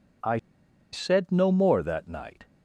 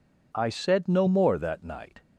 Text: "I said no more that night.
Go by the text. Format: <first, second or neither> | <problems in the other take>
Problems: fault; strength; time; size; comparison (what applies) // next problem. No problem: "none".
second | pauses between "I" and "said"; noticeable; at 0.3 s; 0.56 s long